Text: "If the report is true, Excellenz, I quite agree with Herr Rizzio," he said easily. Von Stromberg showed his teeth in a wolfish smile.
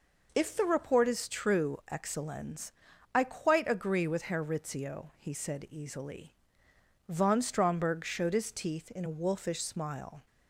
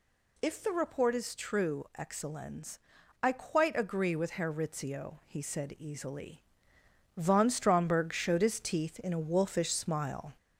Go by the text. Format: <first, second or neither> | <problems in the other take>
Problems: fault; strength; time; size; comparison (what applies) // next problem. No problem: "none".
first | gets louder; slight; throughout; 2.5 dB